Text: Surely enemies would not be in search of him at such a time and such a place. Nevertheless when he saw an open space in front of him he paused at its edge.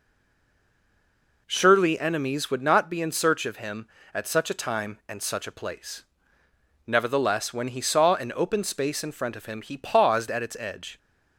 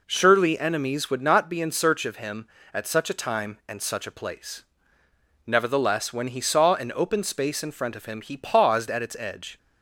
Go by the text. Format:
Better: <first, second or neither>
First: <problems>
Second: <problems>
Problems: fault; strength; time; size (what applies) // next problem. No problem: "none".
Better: second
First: stays silent before the first word; noticeable; until 1.4 s; 1.4 s long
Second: none